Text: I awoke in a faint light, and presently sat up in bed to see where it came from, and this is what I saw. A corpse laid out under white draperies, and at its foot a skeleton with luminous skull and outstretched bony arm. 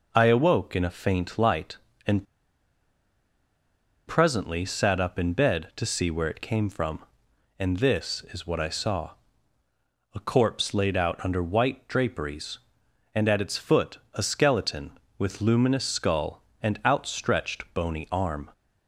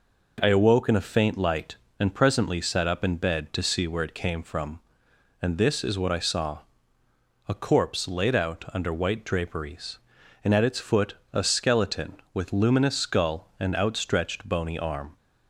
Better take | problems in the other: second | pauses between "and" and "presently"; strong; at 2.2 s; 1.8 s long // pauses between "foot" and "a"; slight; at 13.9 s; 0.16 s long; slight in the second

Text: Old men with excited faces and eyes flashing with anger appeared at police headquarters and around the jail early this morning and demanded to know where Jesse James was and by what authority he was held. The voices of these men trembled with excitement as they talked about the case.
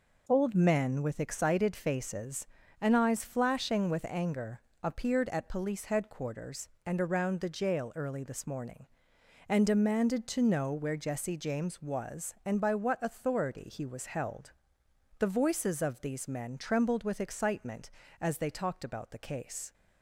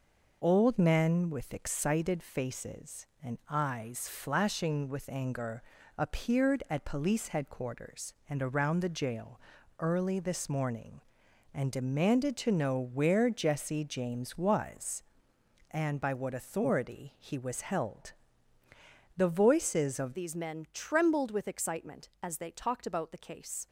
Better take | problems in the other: first | pauses between "anger" and "appeared"; slight; at 5.6 s; 0.36 s long; slight in the first // pauses between "jail" and "early"; at 9.3 s; 0.40 s long // changes voice at "these"; from 20.1 s on; 3.5 s long

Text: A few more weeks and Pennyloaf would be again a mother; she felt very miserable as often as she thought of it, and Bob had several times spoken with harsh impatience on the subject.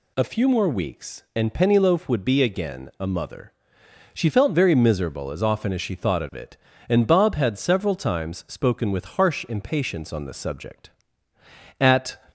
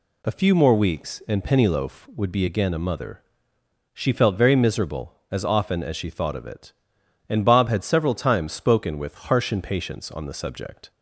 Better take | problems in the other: second | goes on to say "At"; slight; from 11.8 s on; 0.38 s long

